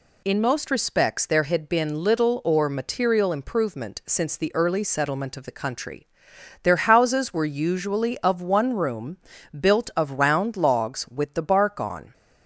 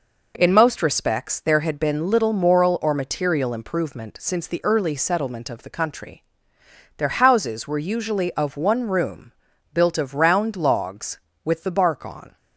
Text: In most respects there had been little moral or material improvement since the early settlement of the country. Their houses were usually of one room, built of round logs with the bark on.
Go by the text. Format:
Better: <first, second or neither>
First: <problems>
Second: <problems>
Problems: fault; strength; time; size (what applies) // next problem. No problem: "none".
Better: second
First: skips "moral"; at 2.4 s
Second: none